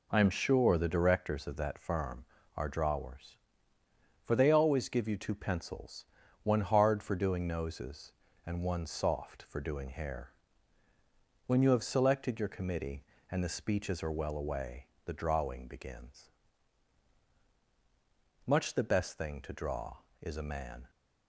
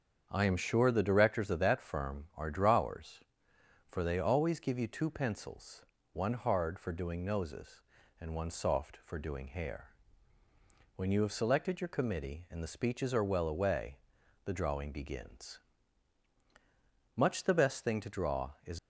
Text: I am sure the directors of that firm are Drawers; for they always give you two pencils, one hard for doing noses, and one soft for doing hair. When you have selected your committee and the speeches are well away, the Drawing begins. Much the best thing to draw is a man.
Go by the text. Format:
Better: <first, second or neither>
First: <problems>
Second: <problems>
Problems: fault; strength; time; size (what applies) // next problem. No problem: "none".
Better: first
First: none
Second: starts louder than the rest; strong; until 1.3 s; 7.5 dB // stops before "a man"; at 18.7 s